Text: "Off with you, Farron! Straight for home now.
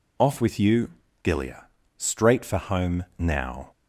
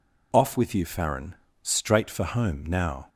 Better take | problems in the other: second | says "Gilia" for "Farron"; at 1.2 s

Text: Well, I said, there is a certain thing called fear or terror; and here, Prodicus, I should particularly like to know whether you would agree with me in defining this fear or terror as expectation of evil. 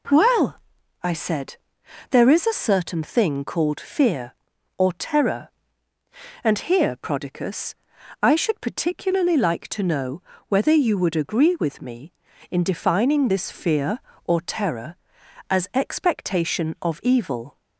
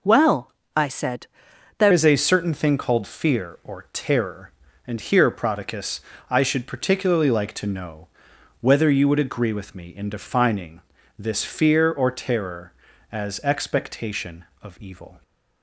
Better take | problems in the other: first | changes voice at "is"; from 1.9 s on; 13.3 s long // pauses between "know" and "whether"; noticeable; at 8.0 s; 0.54 s long; slight in the first // pauses between "defining" and "this"; at 10.7 s; 0.38 s long

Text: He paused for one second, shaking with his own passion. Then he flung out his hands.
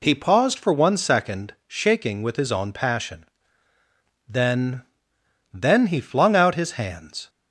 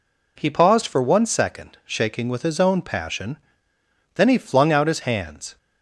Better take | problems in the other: second | says "Then" twice; at 5.5 s

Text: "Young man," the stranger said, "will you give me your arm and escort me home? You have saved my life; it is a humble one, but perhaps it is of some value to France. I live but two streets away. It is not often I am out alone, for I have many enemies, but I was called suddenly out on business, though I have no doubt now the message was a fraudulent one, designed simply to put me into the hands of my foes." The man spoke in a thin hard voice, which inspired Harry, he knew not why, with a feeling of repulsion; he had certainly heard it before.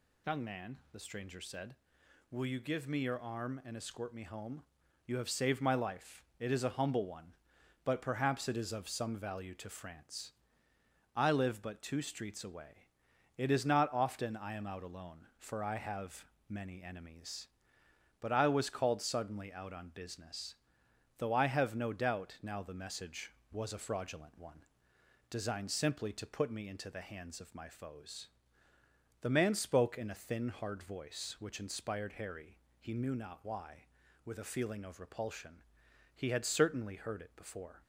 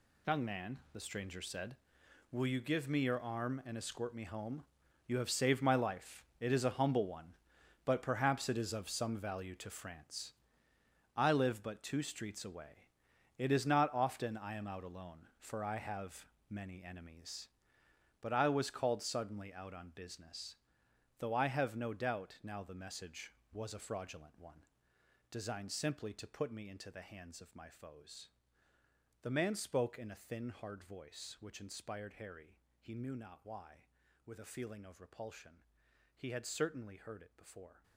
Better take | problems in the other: first | gets quieter; strong; throughout; 13 dB // pauses between "have" and "many"; slight; at 16.2 s; 0.22 s long; slight in the first

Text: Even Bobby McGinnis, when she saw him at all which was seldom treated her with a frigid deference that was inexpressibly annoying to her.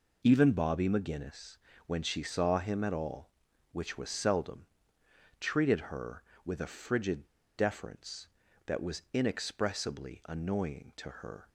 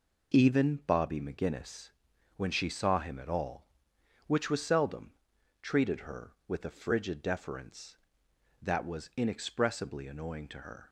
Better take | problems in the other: second | pauses between "seldom" and "treated"; noticeable; at 4.6 s; 0.74 s long; noticeable in the second // pauses between "frigid" and "deference"; slight; at 7.2 s; 0.31 s long

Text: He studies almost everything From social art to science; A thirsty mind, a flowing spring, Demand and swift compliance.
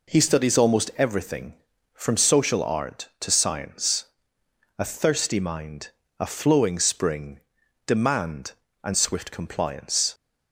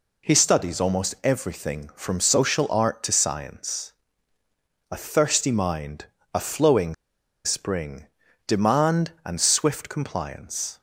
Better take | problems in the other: first | pauses between "flowing" and "spring"; noticeable; at 6.9 s; 0.50 s long

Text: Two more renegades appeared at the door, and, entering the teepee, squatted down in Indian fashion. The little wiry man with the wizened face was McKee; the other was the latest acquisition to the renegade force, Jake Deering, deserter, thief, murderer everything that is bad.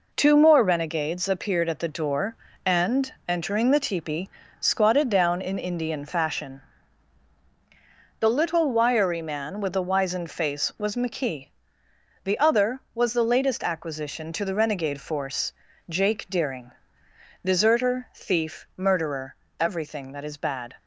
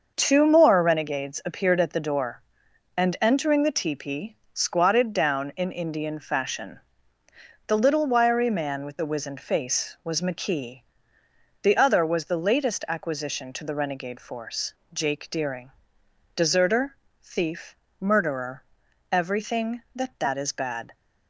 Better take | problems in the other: first | starts louder than the rest; until 1.1 s; 6 dB // pauses between "murderer" and "everything"; noticeable; at 18.6 s; 0.48 s long; slight in the first // says "that" twice; at 20.1 s

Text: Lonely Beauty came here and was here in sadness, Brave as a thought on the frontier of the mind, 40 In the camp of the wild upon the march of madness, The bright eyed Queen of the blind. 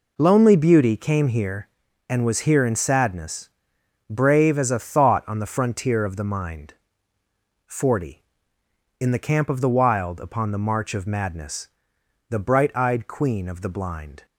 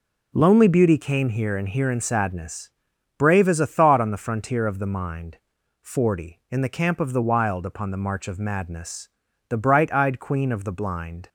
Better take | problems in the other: first | skips "was"; at 1.6 s

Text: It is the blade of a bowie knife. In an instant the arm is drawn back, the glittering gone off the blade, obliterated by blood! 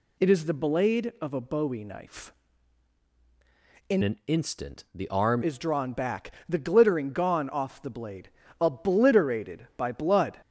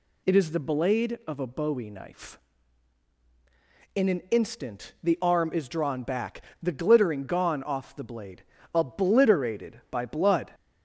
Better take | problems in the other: second | changes voice from "an" to "arm"; from 4.0 to 5.4 s; 1.4 s long

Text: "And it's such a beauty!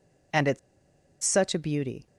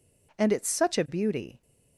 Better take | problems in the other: second | pauses between "it's" and "such"; noticeable; at 0.5 s; 0.64 s long

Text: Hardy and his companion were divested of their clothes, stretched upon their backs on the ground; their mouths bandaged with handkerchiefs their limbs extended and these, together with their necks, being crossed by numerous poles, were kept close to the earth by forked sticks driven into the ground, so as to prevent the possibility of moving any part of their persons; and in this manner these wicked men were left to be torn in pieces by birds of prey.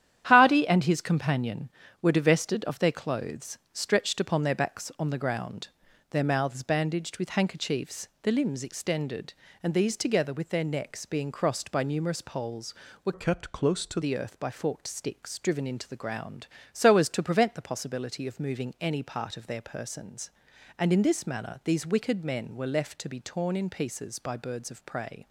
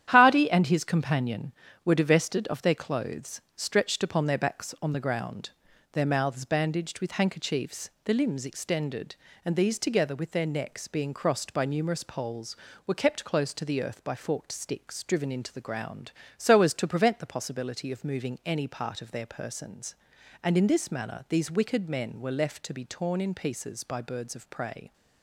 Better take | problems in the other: second | starts louder than the rest; strong; until 1.2 s; 10.5 dB; strong in the second // pauses between "handkerchiefs" and "their"; slight; at 8.0 s; 0.16 s long; slight in the second // changes voice from "kept" to "to"; from 13.1 to 14.0 s; 0.9 s long

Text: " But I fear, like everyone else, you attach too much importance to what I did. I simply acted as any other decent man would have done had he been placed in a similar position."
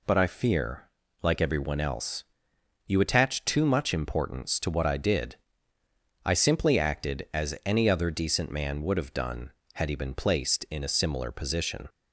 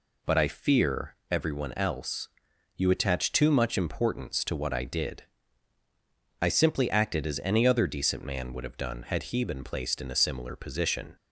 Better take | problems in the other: first | skips "like"; at 1.2 s

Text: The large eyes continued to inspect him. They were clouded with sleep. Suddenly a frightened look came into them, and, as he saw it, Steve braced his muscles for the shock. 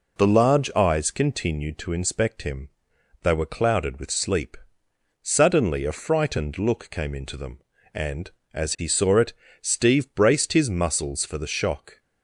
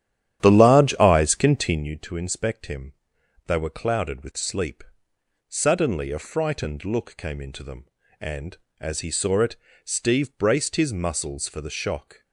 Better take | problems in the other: first | starts louder than the rest; strong; until 2.0 s; 10.5 dB

